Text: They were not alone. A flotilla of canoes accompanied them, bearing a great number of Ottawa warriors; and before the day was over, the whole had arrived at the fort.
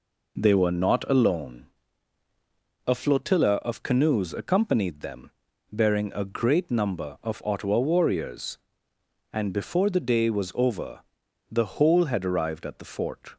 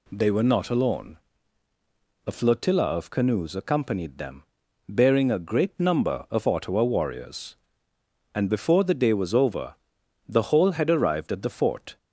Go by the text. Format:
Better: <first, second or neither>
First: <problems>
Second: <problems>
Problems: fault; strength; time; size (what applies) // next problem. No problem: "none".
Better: neither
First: none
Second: none